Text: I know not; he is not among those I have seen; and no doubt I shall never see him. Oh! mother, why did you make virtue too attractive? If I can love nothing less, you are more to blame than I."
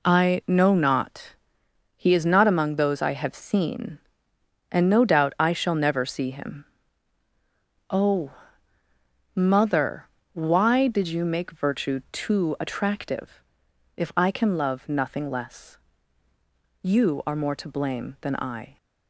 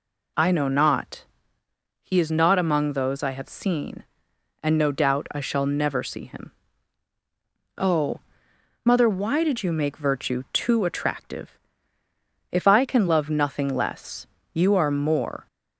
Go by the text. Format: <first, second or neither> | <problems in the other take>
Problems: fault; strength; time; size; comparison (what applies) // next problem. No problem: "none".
first | stops before "to blame than I"; at 15.4 s